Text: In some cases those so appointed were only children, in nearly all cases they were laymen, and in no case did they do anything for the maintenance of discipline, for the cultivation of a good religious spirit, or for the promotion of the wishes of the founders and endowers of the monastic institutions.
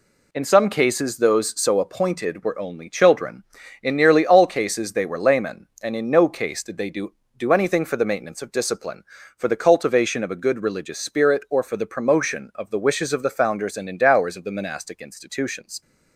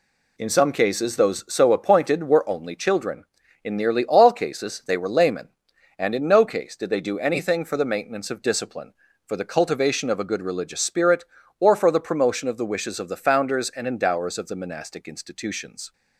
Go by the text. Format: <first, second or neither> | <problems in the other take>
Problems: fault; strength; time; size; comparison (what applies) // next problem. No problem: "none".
second | says "do" twice; at 7.3 s